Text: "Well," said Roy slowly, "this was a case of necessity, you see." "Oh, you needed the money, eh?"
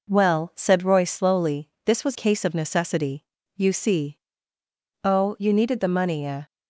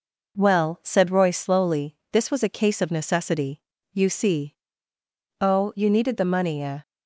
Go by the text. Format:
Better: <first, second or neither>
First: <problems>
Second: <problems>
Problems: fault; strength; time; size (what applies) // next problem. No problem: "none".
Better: second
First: skips "a"; at 2.1 s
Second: none